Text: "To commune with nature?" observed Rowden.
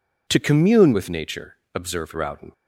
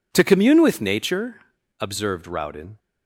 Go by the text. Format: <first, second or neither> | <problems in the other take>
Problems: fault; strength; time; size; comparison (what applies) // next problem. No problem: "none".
neither | none